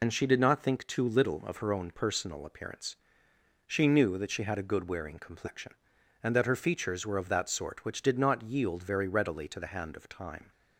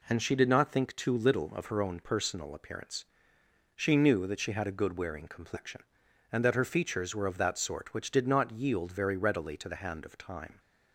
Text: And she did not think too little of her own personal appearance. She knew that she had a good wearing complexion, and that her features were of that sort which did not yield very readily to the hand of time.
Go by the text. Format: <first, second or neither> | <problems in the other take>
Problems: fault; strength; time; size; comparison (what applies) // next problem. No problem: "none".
second | loses the start of "And"; at 0.0 s; 70 ms